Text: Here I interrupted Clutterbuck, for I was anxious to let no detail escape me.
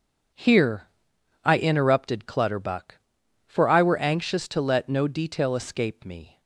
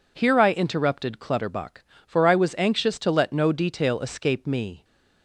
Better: second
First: starts louder than the rest; until 1.9 s; 7 dB // pauses between "Here" and "I"; noticeable; at 0.8 s; 0.56 s long // says "were" for "was"; at 3.8 s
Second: none

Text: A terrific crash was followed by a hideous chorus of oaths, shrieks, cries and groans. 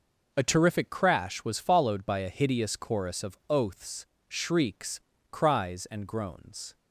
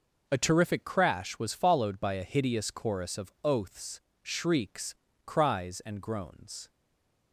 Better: first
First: none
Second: stays silent after the last word; slight; from 6.6 s on; 0.7 s long

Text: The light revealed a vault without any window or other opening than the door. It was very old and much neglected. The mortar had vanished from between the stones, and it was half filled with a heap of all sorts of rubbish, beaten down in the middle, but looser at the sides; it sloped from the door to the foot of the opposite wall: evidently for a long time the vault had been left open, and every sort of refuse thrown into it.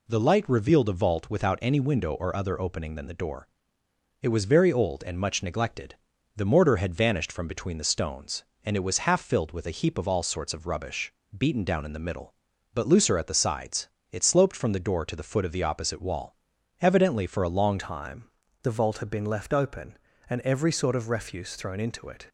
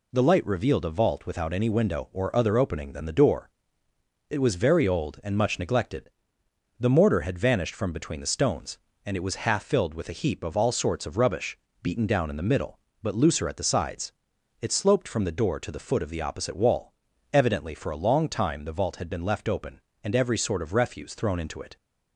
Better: second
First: changes voice at "time"; from 17.7 s on; 4.5 s long // pauses between "time" and "the"; at 18.2 s; 0.38 s long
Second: none

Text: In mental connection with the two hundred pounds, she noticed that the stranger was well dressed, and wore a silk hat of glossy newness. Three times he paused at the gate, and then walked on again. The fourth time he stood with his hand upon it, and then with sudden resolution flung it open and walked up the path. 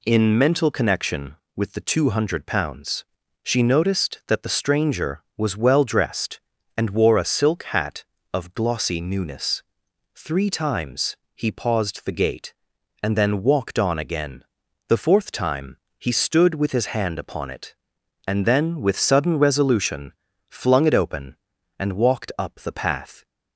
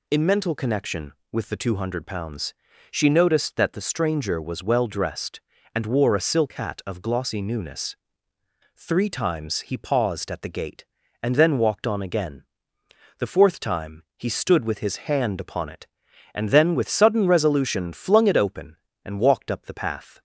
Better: second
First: pauses between "times" and "he"; slight; at 11.1 s; 0.18 s long // skips "at"; at 12.0 s // pauses between "time" and "he"; slight; at 15.7 s; 0.22 s long // pauses between "resolution" and "flung"; slight; at 20.1 s; 0.36 s long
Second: none

